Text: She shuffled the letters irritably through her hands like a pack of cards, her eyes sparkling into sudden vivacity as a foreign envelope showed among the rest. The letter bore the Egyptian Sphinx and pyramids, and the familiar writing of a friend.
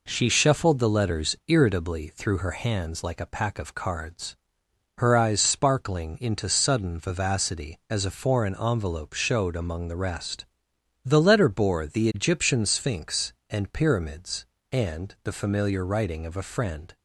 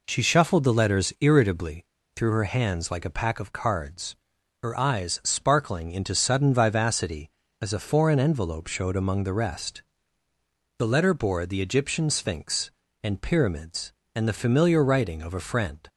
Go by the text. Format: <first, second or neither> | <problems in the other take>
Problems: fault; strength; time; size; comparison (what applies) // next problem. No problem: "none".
first | pauses between "irritably" and "through"; slight; at 1.8 s; 0.29 s long